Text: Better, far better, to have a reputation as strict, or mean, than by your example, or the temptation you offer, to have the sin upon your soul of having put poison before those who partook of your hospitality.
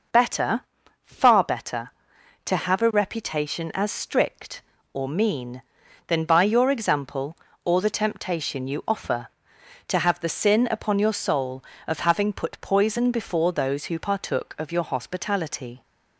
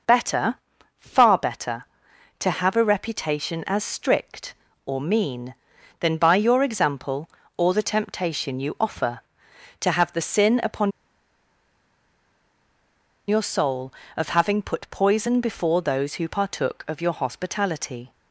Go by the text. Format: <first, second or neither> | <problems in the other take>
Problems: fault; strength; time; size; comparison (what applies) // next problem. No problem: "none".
first | pauses between "upon" and "your"; strong; at 10.9 s; 2.3 s long